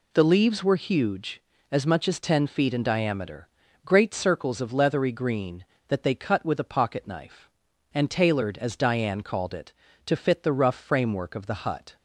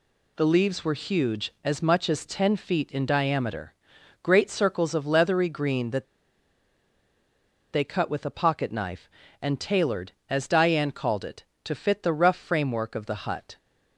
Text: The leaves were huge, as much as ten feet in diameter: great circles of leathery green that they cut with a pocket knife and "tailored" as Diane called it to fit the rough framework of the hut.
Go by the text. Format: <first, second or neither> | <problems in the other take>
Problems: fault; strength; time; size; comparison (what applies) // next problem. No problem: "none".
first | pauses between "that" and "they"; strong; at 6.0 s; 1.6 s long